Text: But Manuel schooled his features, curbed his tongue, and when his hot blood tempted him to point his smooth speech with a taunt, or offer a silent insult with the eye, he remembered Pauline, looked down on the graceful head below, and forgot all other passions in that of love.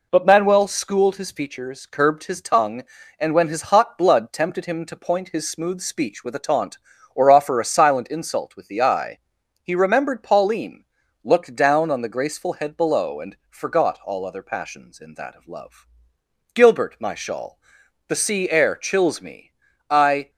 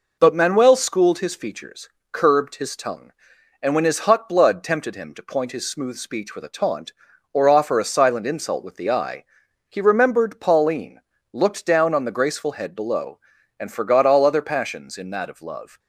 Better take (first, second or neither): second